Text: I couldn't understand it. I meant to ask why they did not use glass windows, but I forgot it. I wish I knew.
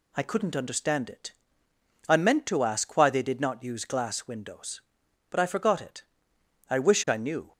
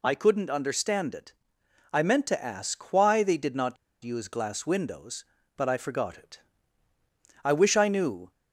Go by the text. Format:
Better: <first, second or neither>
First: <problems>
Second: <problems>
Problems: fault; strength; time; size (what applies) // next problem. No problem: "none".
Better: first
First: none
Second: pauses between "not" and "use"; slight; at 3.7 s; 0.28 s long